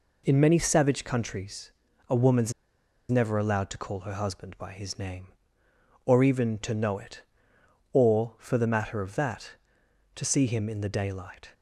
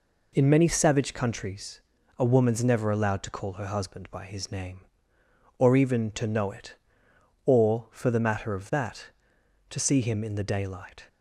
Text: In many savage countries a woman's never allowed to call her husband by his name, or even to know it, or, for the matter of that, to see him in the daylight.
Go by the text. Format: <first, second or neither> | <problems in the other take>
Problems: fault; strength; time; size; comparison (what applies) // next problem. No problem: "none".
second | pauses between "countries" and "a"; at 1.7 s; 0.38 s long; also in the second // pauses between "woman's" and "never"; noticeable; at 2.5 s; 0.58 s long